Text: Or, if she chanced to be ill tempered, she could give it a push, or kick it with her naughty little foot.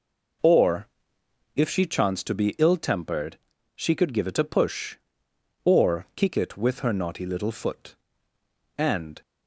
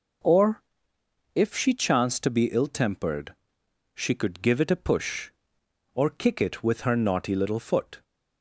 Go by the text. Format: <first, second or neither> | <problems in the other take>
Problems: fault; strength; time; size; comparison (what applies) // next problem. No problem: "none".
second | goes on to say "And"; slight; from 8.7 s on; 0.44 s long